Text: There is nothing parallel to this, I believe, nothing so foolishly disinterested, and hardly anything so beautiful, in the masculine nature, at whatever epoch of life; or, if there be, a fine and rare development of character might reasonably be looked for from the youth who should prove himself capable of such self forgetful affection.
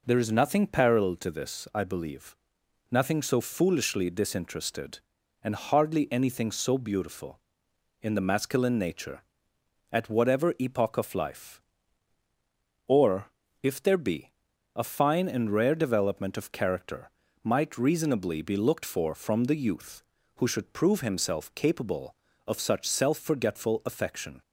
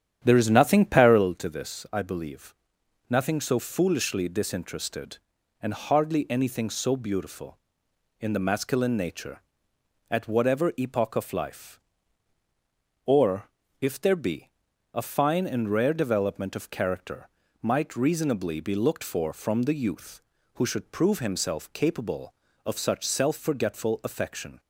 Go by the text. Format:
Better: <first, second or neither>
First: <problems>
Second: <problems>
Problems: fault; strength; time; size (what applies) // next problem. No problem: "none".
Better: first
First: pauses between "character" and "might"; slight; at 17.0 s; 0.34 s long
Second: starts louder than the rest; strong; until 1.4 s; 9.5 dB // pauses between "character" and "might"; slight; at 17.2 s; 0.34 s long